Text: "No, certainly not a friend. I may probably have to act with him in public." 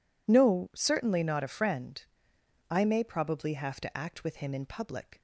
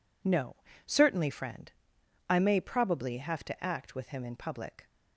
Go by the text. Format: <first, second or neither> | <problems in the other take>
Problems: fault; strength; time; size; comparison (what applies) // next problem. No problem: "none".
first | skips "not a"; at 1.2 s